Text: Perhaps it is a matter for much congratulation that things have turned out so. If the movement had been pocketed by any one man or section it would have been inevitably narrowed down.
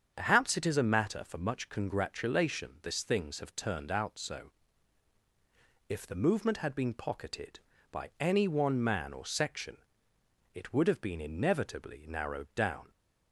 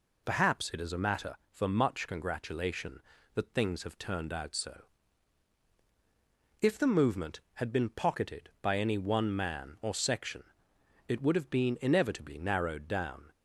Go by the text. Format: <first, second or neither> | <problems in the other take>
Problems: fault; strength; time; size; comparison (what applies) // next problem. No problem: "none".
second | starts louder than the rest; strong; until 1.1 s; 7.5 dB // says "this" for "that"; at 2.8 s // pauses between "section" and "it"; noticeable; at 9.7 s; 0.76 s long; noticeable in the second